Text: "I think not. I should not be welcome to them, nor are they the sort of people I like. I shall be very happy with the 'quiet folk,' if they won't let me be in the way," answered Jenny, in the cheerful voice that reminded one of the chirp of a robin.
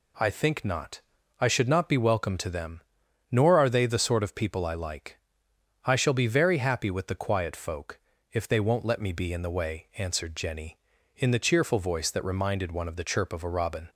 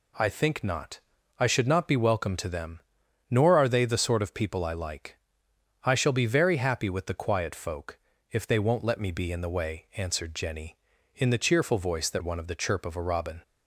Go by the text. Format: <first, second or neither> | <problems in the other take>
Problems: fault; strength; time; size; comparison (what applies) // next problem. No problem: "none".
first | skips "reminded"; at 12.2 s